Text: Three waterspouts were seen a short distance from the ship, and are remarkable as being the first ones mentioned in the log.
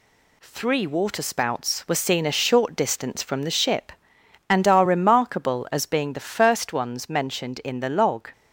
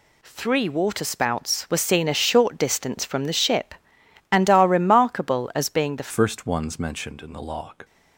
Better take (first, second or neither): first